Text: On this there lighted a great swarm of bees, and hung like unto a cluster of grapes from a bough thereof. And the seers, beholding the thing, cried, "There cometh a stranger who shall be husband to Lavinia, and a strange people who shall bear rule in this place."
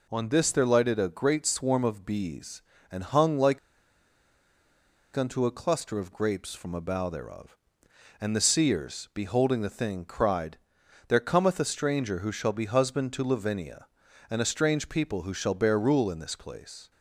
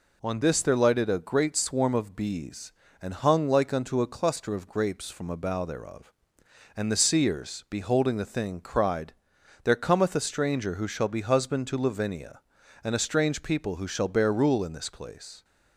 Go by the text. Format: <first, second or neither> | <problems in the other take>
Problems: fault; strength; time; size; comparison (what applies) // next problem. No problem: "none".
second | pauses between "like" and "unto"; strong; at 3.5 s; 1.5 s long